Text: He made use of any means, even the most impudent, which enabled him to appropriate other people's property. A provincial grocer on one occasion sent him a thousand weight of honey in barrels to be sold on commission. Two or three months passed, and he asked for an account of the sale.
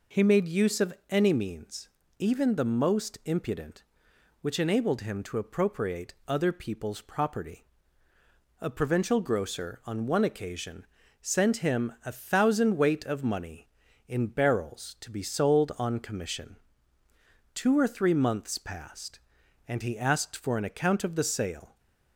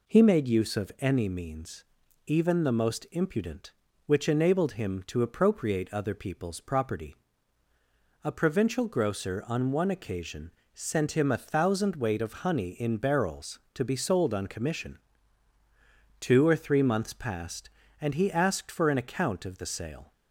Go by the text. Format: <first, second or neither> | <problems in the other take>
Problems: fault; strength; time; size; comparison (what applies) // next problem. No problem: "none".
second | pauses between "of" and "any"; slight; at 0.9 s; 0.16 s long // pauses between "appropriate" and "other"; slight; at 6.1 s; 0.16 s long // pauses between "occasion" and "sent"; slight; at 10.8 s; 0.36 s long; slight in the second // says "money" for "honey"; at 13.2 s